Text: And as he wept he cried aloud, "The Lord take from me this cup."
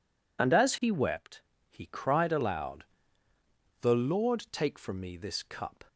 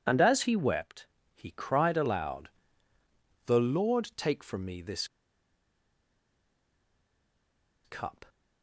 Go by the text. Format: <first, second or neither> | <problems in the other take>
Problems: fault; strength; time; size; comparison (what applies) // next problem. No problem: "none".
first | pauses between "wept" and "he"; slight; at 1.0 s; 0.30 s long; slight in the first // pauses between "this" and "cup"; strong; at 5.0 s; 2.7 s long